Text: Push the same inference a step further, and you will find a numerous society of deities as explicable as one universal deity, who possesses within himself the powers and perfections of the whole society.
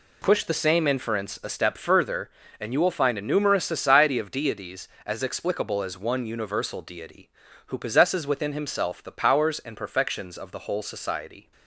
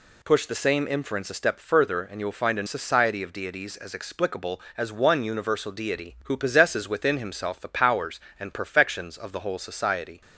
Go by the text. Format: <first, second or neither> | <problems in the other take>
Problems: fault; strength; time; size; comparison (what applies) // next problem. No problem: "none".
first | skips "numerous"; at 2.6 s